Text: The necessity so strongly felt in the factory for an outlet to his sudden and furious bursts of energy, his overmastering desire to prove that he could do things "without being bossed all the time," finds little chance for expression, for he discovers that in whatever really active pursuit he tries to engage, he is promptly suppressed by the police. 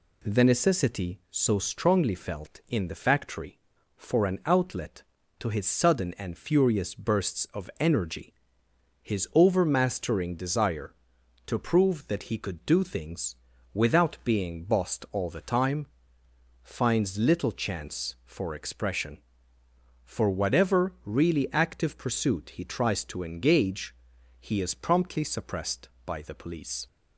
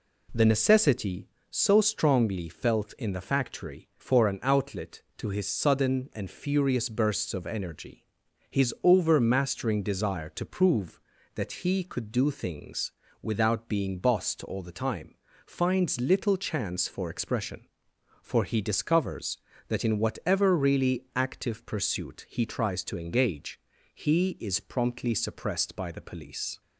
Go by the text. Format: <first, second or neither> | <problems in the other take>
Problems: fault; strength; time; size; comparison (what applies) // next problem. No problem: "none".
second | pauses between "things" and "without"; at 13.3 s; 0.40 s long; slight in the second // skips "he discovers that in"; at 20.3 s